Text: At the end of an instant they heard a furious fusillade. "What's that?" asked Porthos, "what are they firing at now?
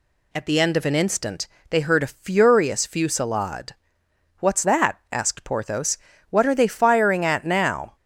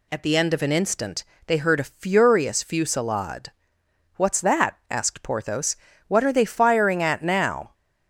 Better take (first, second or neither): neither